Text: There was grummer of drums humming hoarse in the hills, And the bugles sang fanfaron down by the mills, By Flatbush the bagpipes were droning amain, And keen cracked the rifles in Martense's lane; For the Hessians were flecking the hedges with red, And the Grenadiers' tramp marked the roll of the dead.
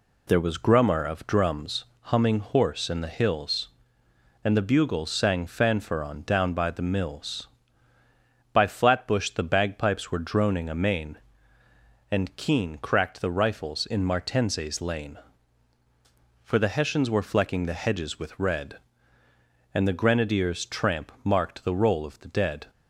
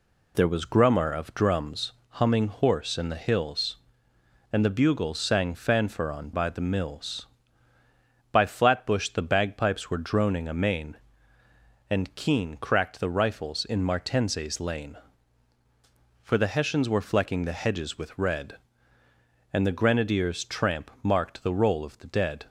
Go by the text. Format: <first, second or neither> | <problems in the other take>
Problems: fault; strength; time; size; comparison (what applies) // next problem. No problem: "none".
first | pauses between "drums" and "humming"; slight; at 1.9 s; 0.18 s long; slight in the first // skips "down"; at 6.3 s